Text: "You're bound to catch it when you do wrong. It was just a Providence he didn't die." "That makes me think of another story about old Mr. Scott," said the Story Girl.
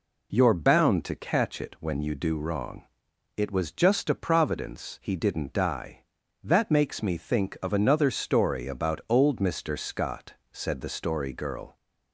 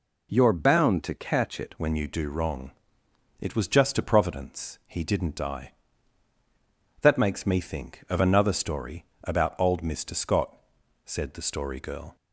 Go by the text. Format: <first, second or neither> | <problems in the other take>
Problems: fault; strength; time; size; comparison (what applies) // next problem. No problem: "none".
first | changes voice at "when"; from 1.7 s on; 10.4 s long // pauses between "story" and "about"; slight; at 9.0 s; 0.18 s long